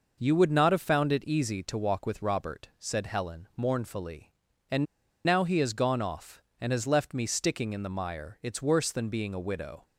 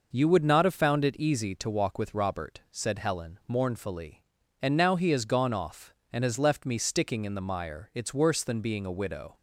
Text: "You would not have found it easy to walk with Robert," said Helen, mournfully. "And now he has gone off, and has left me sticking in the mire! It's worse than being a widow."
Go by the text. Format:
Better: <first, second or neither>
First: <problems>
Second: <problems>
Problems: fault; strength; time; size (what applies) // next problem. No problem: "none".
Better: second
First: pauses between "And" and "now"; at 4.8 s; 0.40 s long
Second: none